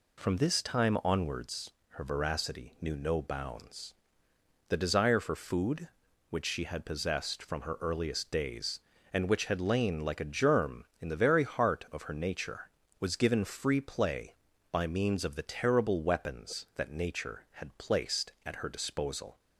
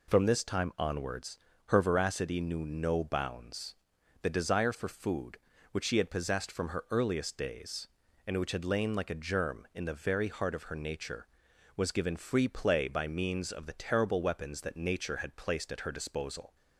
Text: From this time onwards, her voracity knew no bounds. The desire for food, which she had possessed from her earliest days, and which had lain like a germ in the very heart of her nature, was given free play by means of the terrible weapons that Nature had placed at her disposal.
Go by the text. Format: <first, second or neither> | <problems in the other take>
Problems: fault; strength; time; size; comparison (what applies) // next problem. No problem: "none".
neither | none